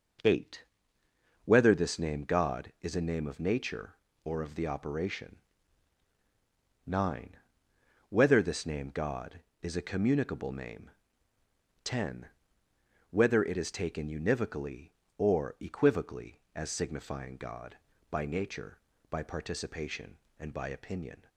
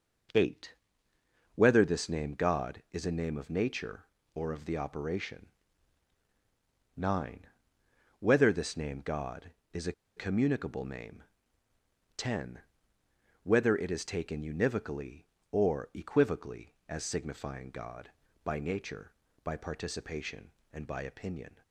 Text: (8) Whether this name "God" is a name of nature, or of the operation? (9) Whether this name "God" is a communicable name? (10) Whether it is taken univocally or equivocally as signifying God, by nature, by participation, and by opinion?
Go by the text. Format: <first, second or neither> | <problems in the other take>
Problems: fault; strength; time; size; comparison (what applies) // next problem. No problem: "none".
first | pauses between "a" and "communicable"; slight; at 9.9 s; 0.24 s long